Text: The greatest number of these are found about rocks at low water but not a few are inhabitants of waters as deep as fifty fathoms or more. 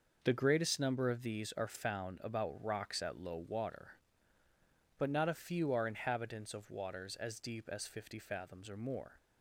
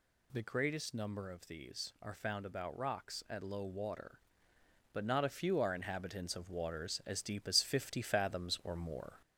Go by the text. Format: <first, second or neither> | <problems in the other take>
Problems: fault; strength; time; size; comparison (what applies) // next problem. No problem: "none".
first | gets louder; slight; throughout; 3 dB